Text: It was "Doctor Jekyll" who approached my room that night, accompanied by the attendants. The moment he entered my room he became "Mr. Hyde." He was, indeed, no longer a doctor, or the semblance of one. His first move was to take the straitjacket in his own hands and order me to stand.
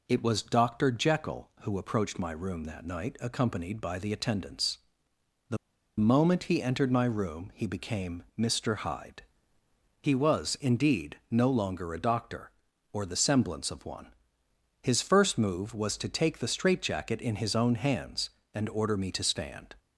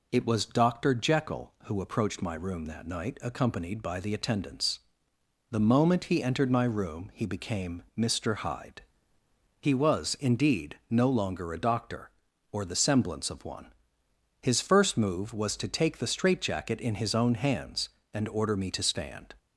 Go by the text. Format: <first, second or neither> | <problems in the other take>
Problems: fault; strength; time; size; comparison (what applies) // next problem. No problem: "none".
second | pauses between "The" and "moment"; at 5.5 s; 0.42 s long